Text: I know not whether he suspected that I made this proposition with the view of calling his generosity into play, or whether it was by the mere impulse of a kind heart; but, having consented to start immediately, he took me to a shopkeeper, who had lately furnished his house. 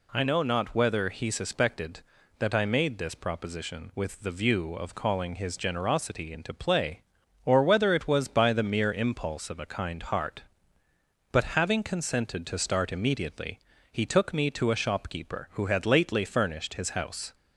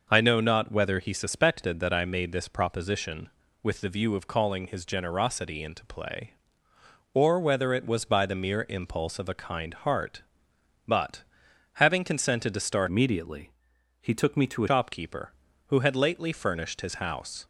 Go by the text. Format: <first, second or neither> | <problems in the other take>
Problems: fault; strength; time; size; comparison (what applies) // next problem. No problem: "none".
first | changes voice from "immediately" to "a"; from 12.8 to 14.6 s; 1.8 s long